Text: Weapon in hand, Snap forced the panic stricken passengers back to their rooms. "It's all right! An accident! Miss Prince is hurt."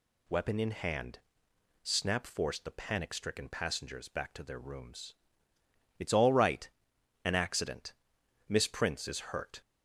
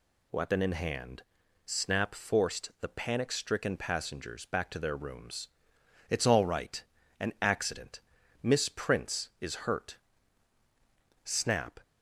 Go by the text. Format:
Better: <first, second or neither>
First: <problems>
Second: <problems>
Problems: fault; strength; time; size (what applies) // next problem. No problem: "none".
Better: first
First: none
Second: goes on to say "Snap"; from 11.2 s on; 0.56 s long